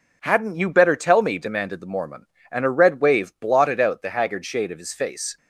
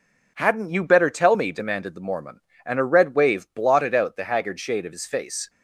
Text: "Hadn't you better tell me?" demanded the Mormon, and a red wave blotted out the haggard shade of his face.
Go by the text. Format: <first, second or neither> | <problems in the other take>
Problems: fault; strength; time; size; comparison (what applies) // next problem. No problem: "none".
neither | none